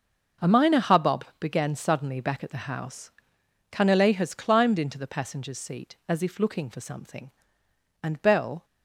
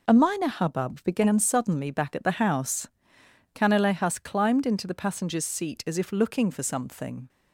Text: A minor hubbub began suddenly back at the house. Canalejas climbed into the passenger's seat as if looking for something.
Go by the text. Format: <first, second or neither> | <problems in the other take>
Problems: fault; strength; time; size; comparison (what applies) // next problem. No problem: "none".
second | starts louder than the rest; until 1.5 s; 6 dB // pauses between "hubbub" and "began"; slight; at 1.2 s; 0.16 s long // goes on to say "And Bell"; noticeable; from 8.0 s on; 0.62 s long